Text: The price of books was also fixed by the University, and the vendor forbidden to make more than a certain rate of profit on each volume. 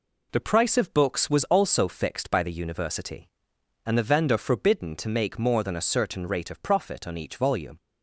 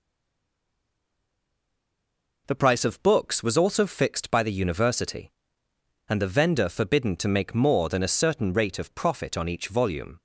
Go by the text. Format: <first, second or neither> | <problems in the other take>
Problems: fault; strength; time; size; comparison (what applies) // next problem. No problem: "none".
first | stays silent before the first word; until 2.4 s; 2.4 s long